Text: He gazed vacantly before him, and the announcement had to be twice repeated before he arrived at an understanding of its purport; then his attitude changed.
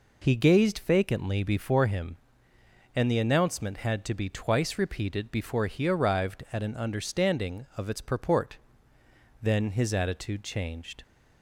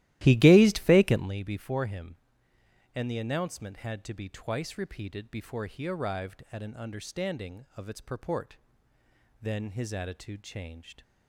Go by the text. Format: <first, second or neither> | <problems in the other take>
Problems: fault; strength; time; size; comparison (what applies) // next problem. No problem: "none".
first | starts louder than the rest; strong; until 1.3 s; 15 dB